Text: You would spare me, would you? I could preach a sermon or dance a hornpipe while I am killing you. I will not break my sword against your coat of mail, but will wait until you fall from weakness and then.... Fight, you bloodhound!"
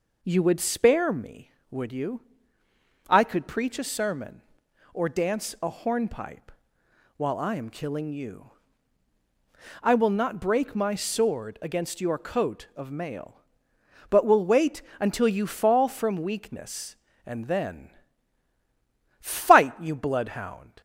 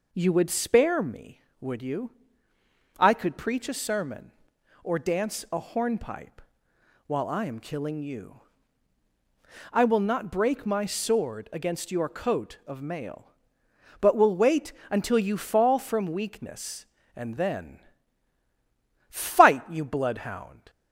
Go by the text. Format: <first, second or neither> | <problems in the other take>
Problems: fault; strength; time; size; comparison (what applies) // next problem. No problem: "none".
neither | pauses between "hornpipe" and "while"; noticeable; the same in both // pauses between "wait" and "until"; slight; the same in both